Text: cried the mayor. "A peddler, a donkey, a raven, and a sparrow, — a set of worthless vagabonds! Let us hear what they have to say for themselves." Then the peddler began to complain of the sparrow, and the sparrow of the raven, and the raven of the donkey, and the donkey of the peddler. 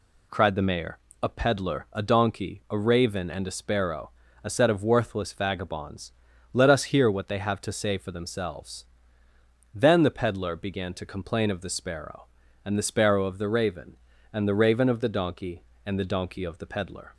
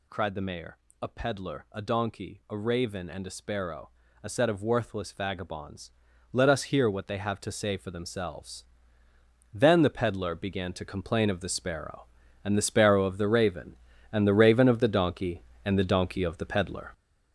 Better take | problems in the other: first | gets louder; strong; throughout; 7.5 dB

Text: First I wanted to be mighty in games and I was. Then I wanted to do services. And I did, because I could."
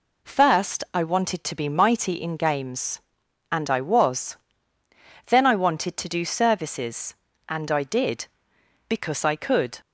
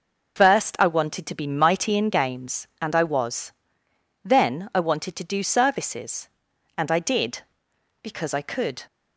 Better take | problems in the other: first | loses the start of "First"; at 0.3 s; 110 ms

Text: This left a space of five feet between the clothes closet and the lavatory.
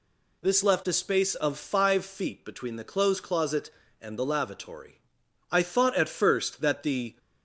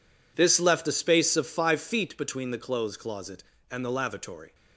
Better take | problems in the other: second | goes on to say "I thought at first that the"; strong; from 5.4 s on; 1.6 s long

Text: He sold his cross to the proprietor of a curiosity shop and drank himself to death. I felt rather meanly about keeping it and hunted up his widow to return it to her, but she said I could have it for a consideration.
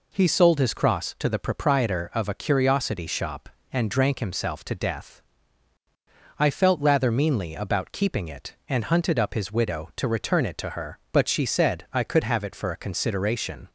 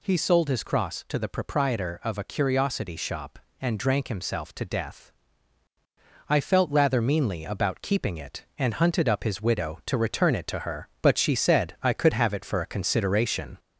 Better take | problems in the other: first | gets louder; slight; throughout; 2.5 dB

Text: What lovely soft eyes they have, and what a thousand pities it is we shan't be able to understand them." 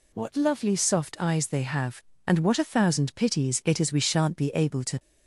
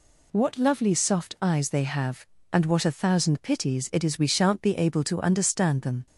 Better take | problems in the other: second | stops before "understand them"; at 4.9 s

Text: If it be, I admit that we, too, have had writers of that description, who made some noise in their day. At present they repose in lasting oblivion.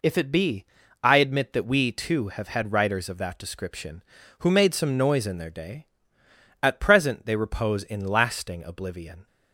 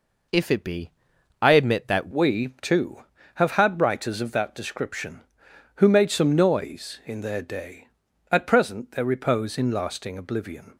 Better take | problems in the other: first | changes voice at "we"; from 2.1 s on; 8.6 s long

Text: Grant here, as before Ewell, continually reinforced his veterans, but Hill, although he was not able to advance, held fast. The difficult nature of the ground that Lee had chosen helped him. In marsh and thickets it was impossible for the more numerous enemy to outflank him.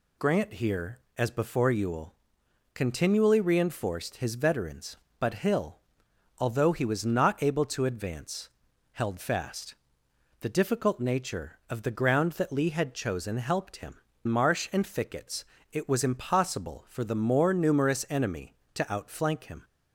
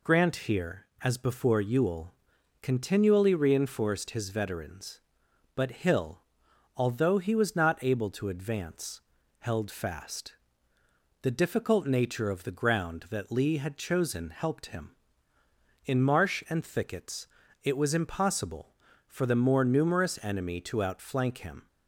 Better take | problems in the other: second | skips "In"; at 14.1 s // pauses between "thickets" and "it"; slight; at 15.4 s; 0.28 s long; slight in the second

